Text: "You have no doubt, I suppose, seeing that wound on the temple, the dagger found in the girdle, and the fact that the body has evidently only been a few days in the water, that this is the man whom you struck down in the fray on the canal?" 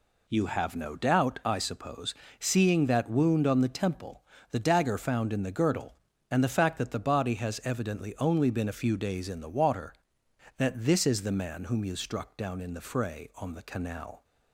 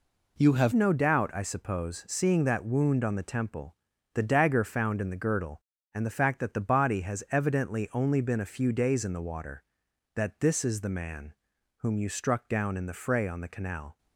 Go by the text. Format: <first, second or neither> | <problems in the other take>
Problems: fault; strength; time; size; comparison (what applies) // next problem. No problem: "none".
first | changes voice at "no"; from 0.7 s on; 13.2 s long // pauses between "man" and "whom"; noticeable; at 11.3 s; 0.46 s long